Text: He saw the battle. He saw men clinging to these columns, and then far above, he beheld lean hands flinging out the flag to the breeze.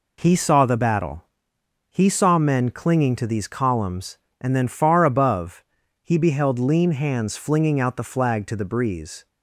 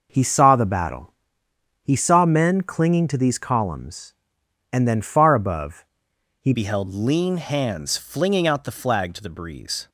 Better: first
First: none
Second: changes voice at "beheld"; from 6.5 s on; 3.3 s long

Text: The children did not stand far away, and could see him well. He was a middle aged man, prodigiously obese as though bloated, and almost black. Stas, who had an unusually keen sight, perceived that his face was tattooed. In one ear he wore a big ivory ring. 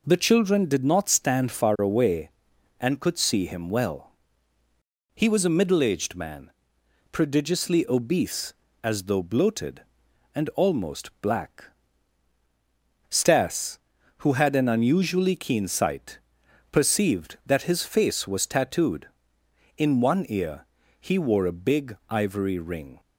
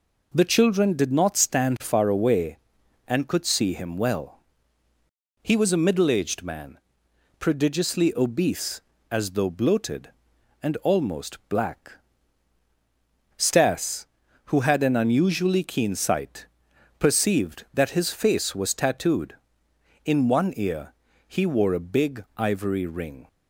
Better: neither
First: pauses between "ear" and "he"; slight; at 20.6 s; 0.34 s long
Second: pauses between "ear" and "he"; slight; at 20.9 s; 0.34 s long

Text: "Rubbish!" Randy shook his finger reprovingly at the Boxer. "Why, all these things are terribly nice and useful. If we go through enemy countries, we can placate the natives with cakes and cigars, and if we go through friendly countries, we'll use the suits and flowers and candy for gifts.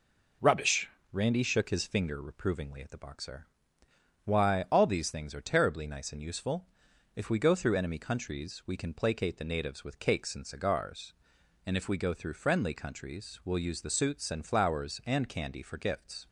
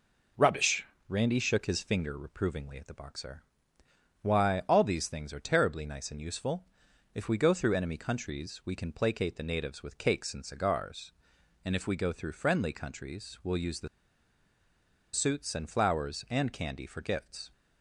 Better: first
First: none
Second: pauses between "the" and "suits"; strong; at 13.8 s; 1.2 s long

